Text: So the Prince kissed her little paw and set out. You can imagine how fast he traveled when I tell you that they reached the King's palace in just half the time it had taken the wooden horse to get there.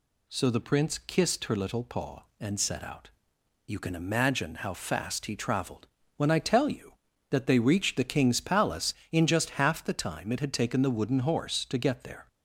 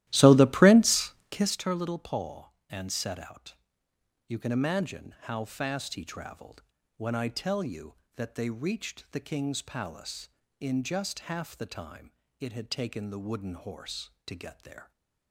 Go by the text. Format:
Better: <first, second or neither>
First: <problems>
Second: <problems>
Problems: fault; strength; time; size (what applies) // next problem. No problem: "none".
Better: first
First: pauses between "traveled" and "when"; slight; at 5.8 s; 0.30 s long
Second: starts louder than the rest; strong; until 1.6 s; 14.5 dB // pauses between "Prince" and "kissed"; slight; at 1.1 s; 0.20 s long // pauses between "traveled" and "when"; slight; at 6.6 s; 0.34 s long // pauses between "time" and "it"; slight; at 12.1 s; 0.28 s long